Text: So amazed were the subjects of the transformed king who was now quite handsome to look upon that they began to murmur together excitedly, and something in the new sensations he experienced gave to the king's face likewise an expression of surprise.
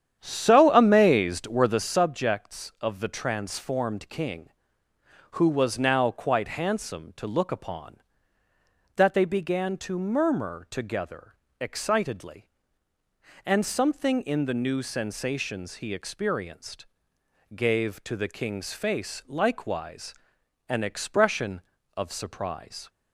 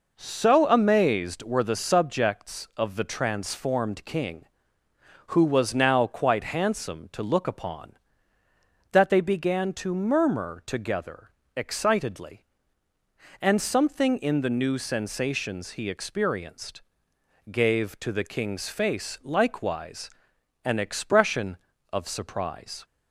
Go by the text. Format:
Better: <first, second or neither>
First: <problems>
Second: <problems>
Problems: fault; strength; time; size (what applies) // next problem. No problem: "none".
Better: second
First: starts louder than the rest; strong; until 1.9 s; 9.5 dB // pauses between "together" and "excitedly"; slight; at 11.3 s; 0.26 s long // pauses between "experienced" and "gave"; noticeable; at 16.8 s; 0.70 s long // pauses between "likewise" and "an"; noticeable; at 20.1 s; 0.54 s long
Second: pauses between "together" and "excitedly"; slight; at 11.3 s; 0.26 s long // pauses between "experienced" and "gave"; noticeable; at 16.8 s; 0.70 s long // pauses between "likewise" and "an"; noticeable; at 20.1 s; 0.54 s long